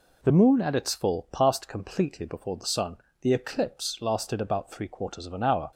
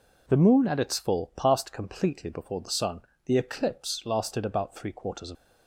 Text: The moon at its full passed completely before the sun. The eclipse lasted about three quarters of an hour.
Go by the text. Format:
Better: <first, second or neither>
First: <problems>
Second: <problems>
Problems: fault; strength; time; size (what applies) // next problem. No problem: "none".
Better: first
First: none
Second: stops before "an hour"; at 5.3 s